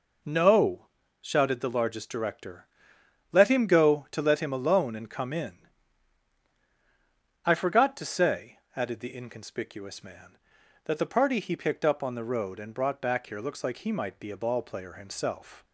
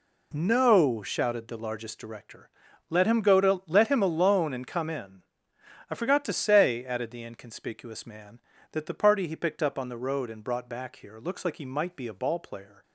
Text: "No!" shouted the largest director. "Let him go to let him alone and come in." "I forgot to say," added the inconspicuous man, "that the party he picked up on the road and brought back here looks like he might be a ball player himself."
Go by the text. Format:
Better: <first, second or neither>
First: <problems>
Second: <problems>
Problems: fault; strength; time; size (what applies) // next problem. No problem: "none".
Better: first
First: none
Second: stops before "himself"; at 12.8 s